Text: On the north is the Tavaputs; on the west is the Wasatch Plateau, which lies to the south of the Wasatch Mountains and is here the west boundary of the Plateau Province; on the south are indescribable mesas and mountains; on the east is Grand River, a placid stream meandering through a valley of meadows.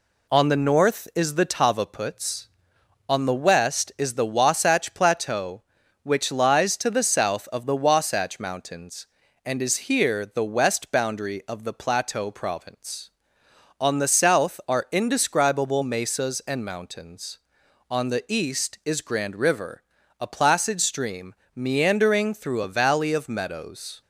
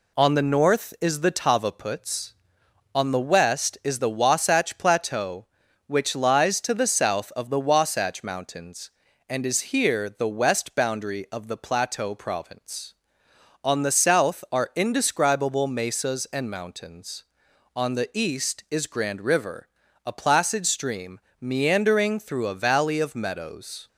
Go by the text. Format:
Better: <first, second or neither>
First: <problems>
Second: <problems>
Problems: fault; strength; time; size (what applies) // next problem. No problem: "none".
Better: neither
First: pauses between "stream" and "meandering"; slight; at 21.3 s; 0.18 s long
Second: pauses between "stream" and "meandering"; slight; at 21.2 s; 0.18 s long